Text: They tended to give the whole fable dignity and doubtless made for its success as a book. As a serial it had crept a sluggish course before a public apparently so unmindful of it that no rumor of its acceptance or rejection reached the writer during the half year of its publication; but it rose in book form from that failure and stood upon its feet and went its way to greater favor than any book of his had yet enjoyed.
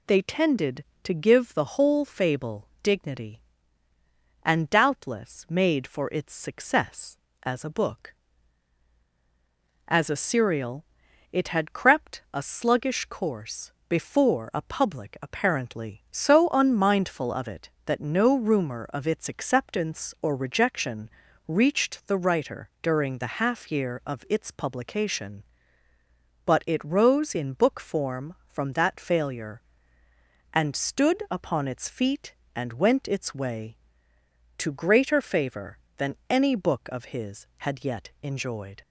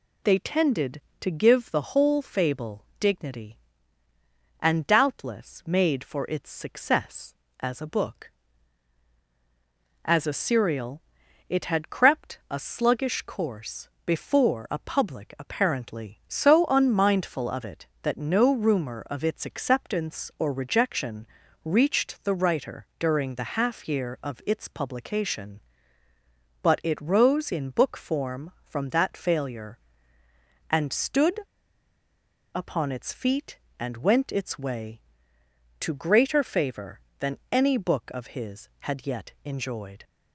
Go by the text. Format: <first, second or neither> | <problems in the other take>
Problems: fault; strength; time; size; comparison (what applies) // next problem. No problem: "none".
first | pauses between "fable" and "dignity"; slight; at 2.8 s; 0.16 s long; slight in the first // pauses between "serial" and "it"; noticeable; at 11.0 s; 0.46 s long; noticeable in the first // pauses between "course" and "before"; slight; at 13.8 s; 0.18 s long; slight in the first // pauses between "rejection" and "reached"; at 21.2 s; 0.38 s long; also in the first // pauses between "stood" and "upon"; at 31.3 s; 1.1 s long